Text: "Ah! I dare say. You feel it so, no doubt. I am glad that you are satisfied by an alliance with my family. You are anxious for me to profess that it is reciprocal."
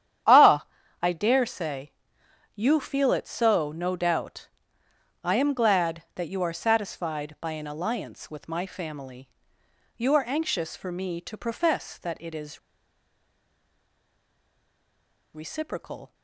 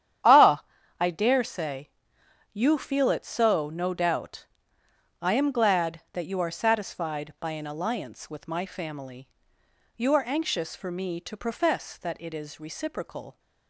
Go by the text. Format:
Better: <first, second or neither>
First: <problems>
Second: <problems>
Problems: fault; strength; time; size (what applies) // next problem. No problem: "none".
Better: second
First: starts louder than the rest; strong; until 1.6 s; 10 dB // pauses between "is" and "reciprocal"; strong; at 12.5 s; 2.7 s long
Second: starts louder than the rest; strong; until 1.5 s; 10 dB